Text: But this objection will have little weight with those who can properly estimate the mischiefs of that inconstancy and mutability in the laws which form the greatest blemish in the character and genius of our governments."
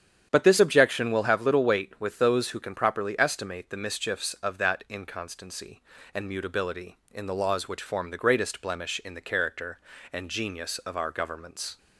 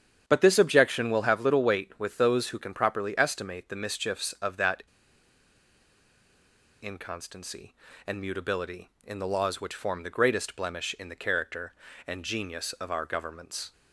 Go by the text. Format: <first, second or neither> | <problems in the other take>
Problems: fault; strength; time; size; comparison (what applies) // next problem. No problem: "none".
first | starts louder than the rest; strong; until 1.2 s; 8.5 dB; strong in the first // pauses between "that" and "inconstancy"; strong; at 4.8 s; 1.9 s long